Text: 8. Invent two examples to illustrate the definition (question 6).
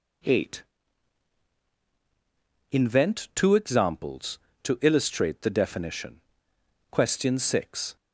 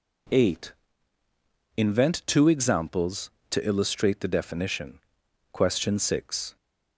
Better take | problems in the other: neither | none

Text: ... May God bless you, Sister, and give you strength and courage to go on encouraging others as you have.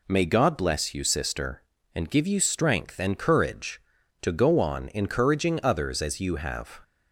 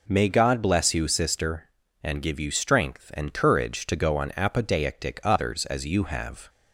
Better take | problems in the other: first | says "apodeictic" for "encouraging"; at 4.3 s

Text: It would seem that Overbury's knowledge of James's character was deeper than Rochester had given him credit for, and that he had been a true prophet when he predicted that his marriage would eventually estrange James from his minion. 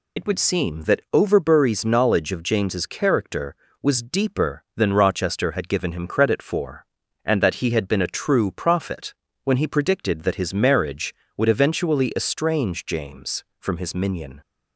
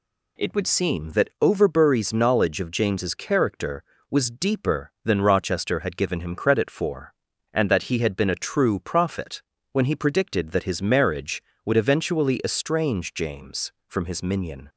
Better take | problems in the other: second | loses the start of "It"; at 0.1 s; 80 ms // pauses between "prophet" and "when"; slight; at 9.1 s; 0.32 s long; slight in the second

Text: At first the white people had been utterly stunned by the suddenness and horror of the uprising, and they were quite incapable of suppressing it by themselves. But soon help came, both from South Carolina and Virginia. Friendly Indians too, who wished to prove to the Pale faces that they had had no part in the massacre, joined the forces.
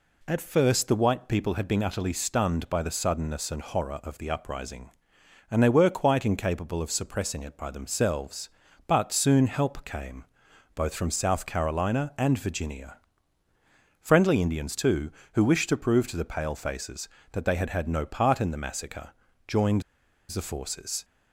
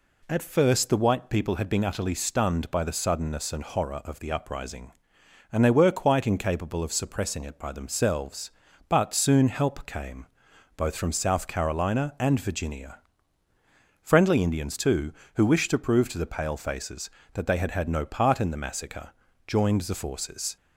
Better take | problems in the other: second | pauses between "joined" and "the"; noticeable; at 19.8 s; 0.47 s long

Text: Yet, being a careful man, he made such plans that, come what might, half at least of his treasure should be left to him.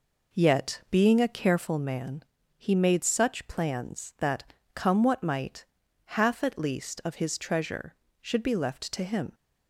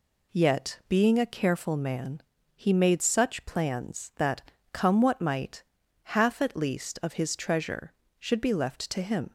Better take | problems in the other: second | starts louder than the rest; noticeable; until 1.8 s; 4.5 dB

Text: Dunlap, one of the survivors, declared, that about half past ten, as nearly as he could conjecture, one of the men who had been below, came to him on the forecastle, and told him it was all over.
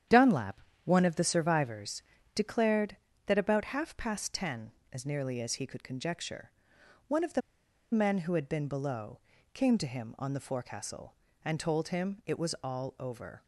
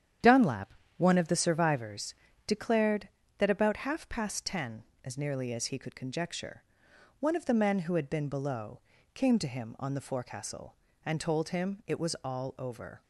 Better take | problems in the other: second | starts louder than the rest; strong; until 1.3 s; 9.5 dB; strong in the second // pauses between "the" and "men"; noticeable; at 7.4 s; 0.52 s long

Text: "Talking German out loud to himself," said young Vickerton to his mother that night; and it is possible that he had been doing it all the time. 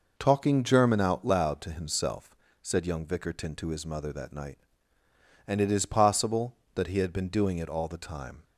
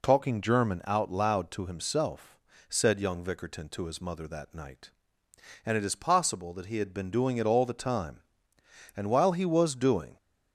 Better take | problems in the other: first | goes on to say "And while he was doing"; noticeable; from 8.9 s on; 1.2 s long

